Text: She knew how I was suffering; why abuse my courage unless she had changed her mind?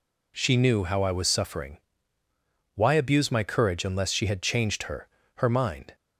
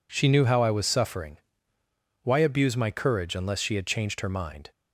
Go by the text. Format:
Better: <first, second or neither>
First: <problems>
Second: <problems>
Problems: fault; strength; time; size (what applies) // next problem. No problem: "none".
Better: second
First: says "her" twice; at 5.3 s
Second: none